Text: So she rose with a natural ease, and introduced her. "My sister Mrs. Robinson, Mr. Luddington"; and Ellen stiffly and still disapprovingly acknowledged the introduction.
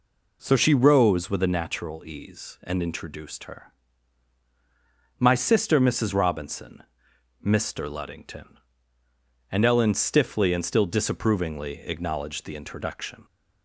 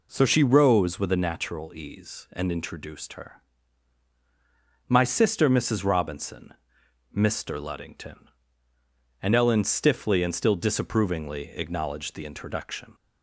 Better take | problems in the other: neither | none

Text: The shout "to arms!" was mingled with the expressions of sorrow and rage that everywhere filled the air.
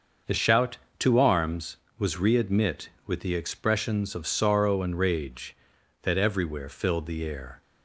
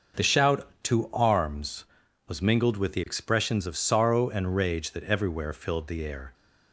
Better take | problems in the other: second | starts louder than the rest; until 1.4 s; 6.5 dB // says "readmit" for "mingled"; at 2.1 s

